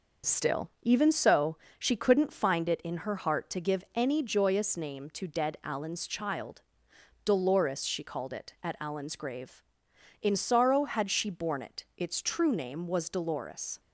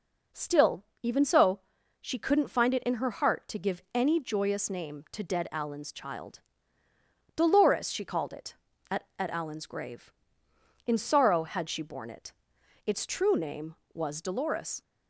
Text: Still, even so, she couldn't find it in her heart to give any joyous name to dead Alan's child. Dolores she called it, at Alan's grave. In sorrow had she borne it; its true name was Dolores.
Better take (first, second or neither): first